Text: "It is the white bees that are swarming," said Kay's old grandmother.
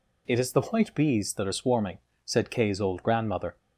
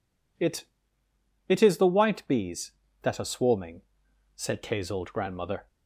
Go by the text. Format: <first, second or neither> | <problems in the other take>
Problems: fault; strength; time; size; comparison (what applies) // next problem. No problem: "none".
first | says "It" twice; at 1.4 s